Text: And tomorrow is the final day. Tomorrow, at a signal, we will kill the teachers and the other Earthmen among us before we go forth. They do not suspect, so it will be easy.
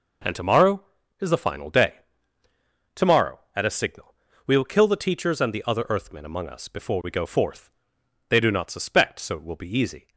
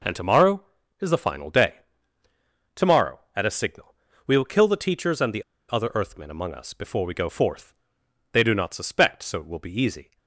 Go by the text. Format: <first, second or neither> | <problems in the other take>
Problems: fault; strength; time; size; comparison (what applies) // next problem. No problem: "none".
first | pauses between "the" and "other"; slight; at 5.4 s; 0.28 s long